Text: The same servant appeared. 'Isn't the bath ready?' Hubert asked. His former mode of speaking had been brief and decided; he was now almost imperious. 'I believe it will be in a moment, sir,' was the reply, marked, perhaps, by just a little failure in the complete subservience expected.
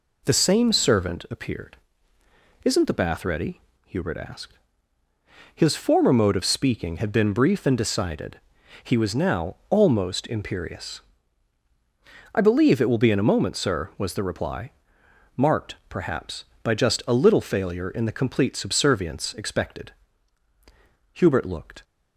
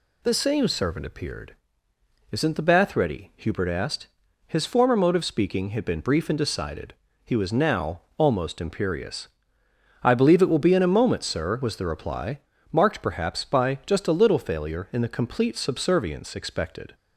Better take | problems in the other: second | goes on to say "Hubert looked"; noticeable; from 21.1 s on; 0.72 s long

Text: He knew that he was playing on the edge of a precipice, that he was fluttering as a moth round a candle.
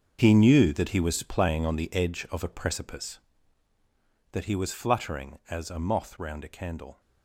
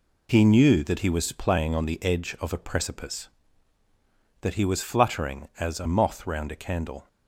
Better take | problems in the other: second | gets quieter; strong; throughout; 13 dB

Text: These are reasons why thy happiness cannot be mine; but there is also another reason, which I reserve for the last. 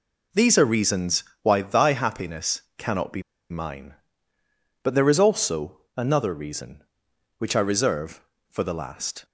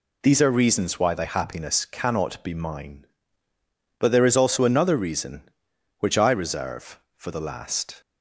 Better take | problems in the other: second | pauses between "reasons" and "why"; slight; at 1.2 s; 0.18 s long // pauses between "happiness" and "cannot"; slight; at 2.6 s; 0.16 s long // pauses between "be" and "mine"; slight; at 3.2 s; 0.29 s long // pauses between "also" and "another"; slight; at 5.7 s; 0.18 s long

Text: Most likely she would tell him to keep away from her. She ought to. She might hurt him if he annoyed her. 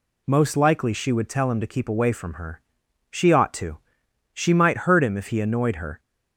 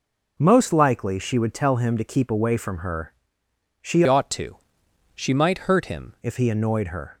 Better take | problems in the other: first | changes voice from "ought" to "him"; from 4.0 to 6.1 s; 2.1 s long

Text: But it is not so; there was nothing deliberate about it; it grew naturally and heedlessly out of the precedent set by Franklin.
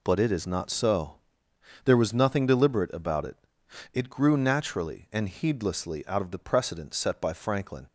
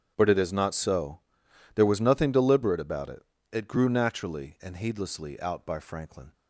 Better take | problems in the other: first | starts louder than the rest; strong; until 1.1 s; 7.5 dB // skips "of the precedent set"; at 5.6 s

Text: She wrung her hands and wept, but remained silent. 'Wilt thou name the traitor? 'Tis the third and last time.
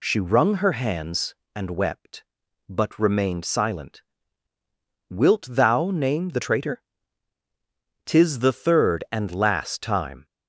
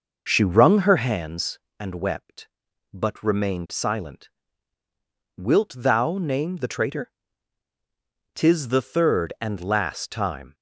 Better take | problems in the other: first | starts louder than the rest; noticeable; until 1.2 s; 5.5 dB

